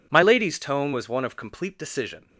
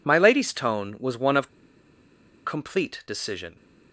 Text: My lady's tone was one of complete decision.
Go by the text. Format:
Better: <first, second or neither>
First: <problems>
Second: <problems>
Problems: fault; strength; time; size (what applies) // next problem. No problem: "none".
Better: first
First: none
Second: pauses between "of" and "complete"; at 1.4 s; 0.99 s long